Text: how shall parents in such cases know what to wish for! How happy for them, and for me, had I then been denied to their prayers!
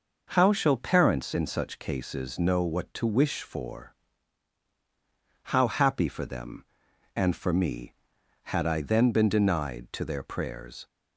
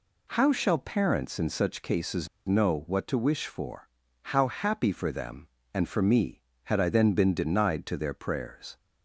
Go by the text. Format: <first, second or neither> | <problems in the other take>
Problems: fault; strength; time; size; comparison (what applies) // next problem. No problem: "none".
first | pauses between "cases" and "know"; slight; at 2.2 s; 0.18 s long